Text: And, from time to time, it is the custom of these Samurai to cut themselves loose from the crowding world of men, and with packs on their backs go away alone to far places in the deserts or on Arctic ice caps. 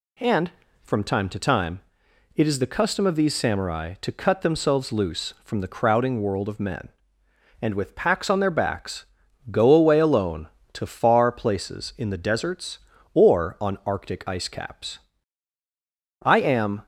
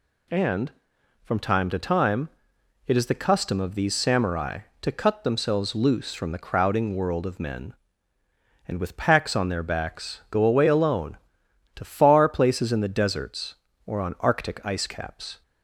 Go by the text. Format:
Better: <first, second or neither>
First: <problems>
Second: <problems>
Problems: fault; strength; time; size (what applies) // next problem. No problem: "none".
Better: second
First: pauses between "backs" and "go"; noticeable; at 9.0 s; 0.46 s long // goes on to say "I am"; noticeable; from 16.2 s on; 0.64 s long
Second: none